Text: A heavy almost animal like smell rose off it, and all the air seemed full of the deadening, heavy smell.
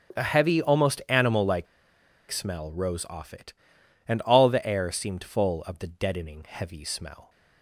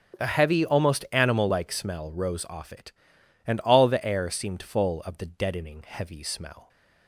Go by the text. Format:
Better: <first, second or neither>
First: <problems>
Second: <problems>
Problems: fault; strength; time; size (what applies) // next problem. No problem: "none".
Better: second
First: starts louder than the rest; strong; until 1.2 s; 8 dB // pauses between "like" and "smell"; noticeable; at 1.6 s; 0.65 s long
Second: starts louder than the rest; strong; until 1.2 s; 8 dB